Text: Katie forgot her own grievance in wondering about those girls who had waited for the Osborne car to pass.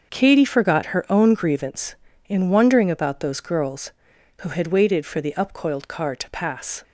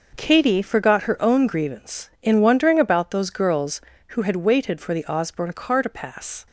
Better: second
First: starts louder than the rest; until 1.1 s; 6.5 dB // says "Upcoiled" for "Osborne"; at 5.3 s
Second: none

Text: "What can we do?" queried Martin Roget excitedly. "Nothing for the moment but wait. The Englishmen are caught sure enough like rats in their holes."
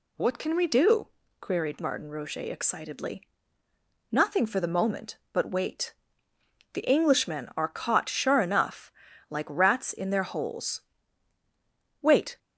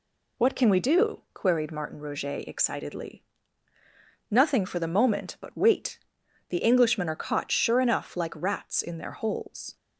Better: second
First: pauses between "enough" and "like"; slight; at 8.9 s; 0.36 s long // goes on to say "Wait"; slight; from 12.0 s on; 0.38 s long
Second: none

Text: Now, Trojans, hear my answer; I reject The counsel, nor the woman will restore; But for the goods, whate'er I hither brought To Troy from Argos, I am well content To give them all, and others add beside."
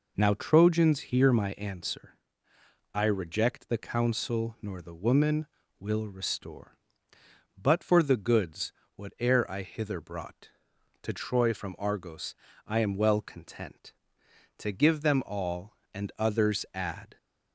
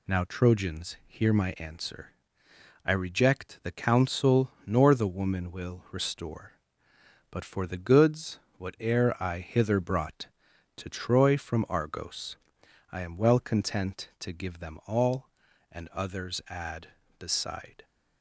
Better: second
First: stops before "beside"; at 17.1 s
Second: none

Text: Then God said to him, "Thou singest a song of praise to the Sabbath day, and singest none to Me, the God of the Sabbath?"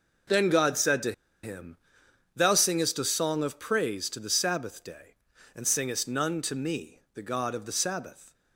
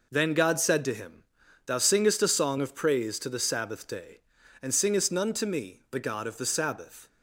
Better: second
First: pauses between "to" and "him"; slight; at 1.1 s; 0.31 s long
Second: none

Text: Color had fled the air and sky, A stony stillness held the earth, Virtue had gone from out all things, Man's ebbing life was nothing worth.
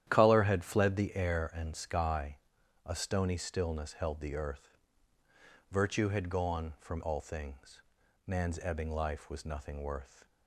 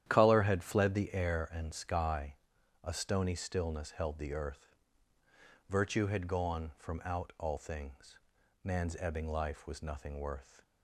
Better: second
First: starts louder than the rest; strong; until 1.1 s; 11 dB // skips "out"; at 7.0 s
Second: starts louder than the rest; strong; until 1.1 s; 11 dB

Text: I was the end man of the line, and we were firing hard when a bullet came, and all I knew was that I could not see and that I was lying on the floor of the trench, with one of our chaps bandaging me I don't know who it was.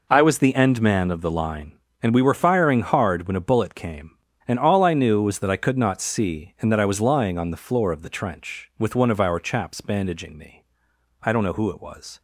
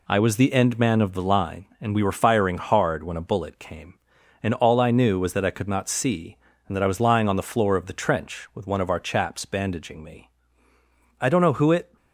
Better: first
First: pauses between "me" and "I"; noticeable; at 10.6 s; 0.60 s long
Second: pauses between "me" and "I"; noticeable; at 10.2 s; 0.90 s long // stops before "was"; at 11.9 s

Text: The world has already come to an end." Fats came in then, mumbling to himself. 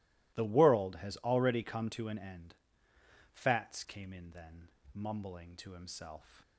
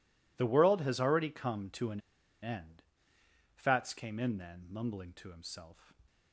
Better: first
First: none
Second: pauses between "an" and "end"; at 2.0 s; 0.41 s long

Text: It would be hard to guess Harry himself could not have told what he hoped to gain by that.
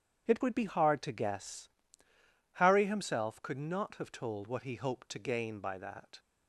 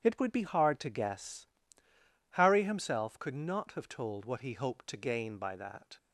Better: neither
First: starts louder than the rest; strong; until 1.3 s; 8.5 dB // pauses between "guess" and "Harry"; noticeable; at 1.7 s; 0.84 s long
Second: starts louder than the rest; strong; until 1.0 s; 8.5 dB // pauses between "guess" and "Harry"; noticeable; at 1.4 s; 0.84 s long

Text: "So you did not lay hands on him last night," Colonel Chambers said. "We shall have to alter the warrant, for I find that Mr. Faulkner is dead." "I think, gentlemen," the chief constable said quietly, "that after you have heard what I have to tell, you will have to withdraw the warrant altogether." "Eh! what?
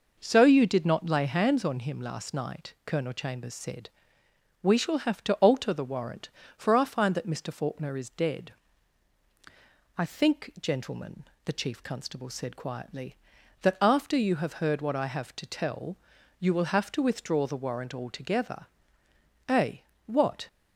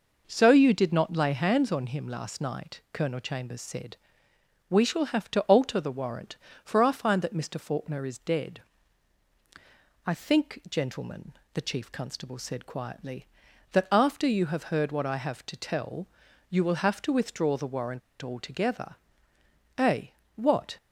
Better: first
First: none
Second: pauses between "warrant" and "altogether"; slight; at 18.0 s; 0.21 s long

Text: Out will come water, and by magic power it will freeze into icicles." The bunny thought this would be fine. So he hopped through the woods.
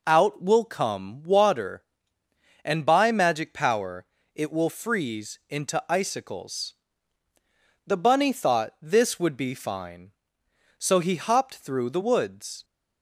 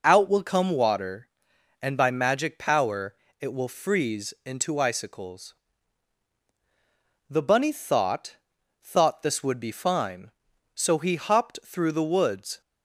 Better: first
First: pauses between "power" and "it"; slight; at 4.0 s; 0.30 s long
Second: pauses between "power" and "it"; slight; at 3.1 s; 0.24 s long // says "thought" twice; at 8.8 s

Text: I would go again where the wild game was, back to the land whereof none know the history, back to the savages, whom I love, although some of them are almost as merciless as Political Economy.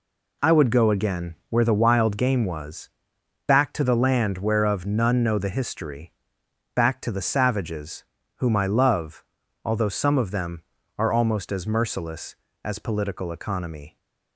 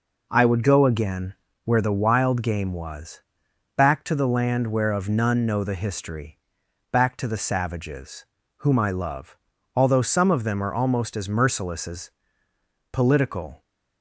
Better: first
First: none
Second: pauses between "again" and "where"; slight; at 1.3 s; 0.30 s long // pauses between "as" and "Political"; noticeable; at 12.1 s; 0.82 s long // stops before "Economy"; at 13.6 s

